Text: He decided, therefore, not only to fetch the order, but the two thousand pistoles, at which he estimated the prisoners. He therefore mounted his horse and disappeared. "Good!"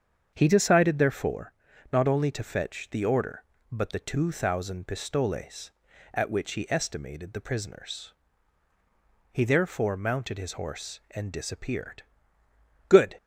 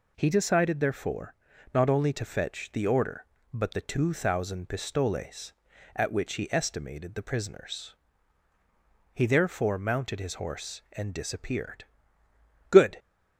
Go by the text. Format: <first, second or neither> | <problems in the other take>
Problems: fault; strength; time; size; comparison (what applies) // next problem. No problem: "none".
second | starts louder than the rest; strong; until 1.4 s; 7.5 dB